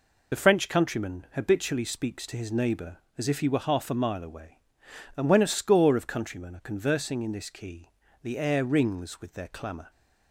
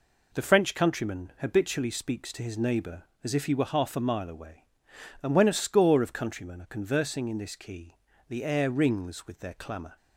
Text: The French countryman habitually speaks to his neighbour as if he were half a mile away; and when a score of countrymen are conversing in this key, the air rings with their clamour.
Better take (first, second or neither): second